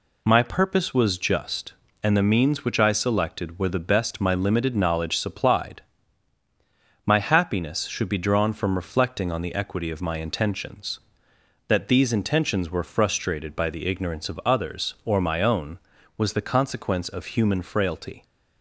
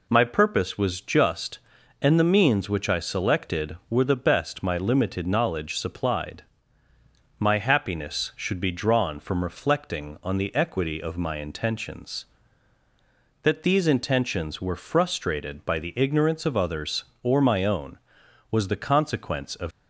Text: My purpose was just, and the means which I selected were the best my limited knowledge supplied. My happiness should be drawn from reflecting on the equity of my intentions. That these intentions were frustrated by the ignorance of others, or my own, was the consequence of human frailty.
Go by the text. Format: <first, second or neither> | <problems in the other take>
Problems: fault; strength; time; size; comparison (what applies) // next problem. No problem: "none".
first | stops before "human frailty"; at 19.7 s